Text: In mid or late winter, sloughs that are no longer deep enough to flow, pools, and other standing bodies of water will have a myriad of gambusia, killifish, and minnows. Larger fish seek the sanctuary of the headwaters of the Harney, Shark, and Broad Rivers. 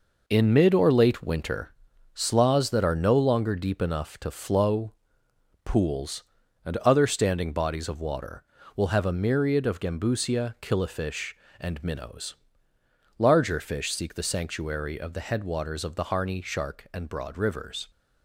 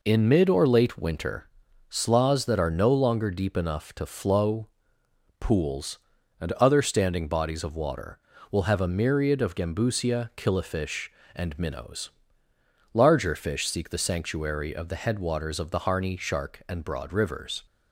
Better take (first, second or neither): second